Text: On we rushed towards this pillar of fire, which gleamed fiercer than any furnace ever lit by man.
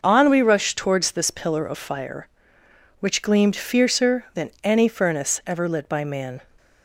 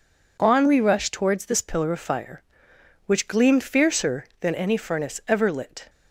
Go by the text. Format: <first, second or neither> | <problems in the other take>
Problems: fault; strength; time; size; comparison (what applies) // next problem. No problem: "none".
first | stops before "by man"; at 5.8 s